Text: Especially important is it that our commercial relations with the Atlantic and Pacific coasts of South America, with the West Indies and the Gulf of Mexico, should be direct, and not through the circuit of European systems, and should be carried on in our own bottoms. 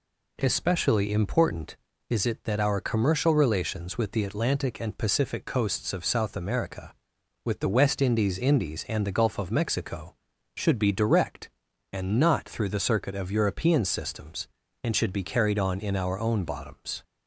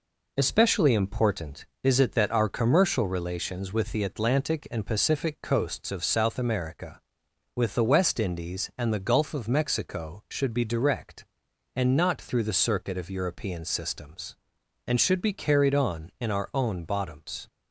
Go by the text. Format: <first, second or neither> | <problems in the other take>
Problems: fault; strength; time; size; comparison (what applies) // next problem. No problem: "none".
second | says "Indies" twice; at 8.3 s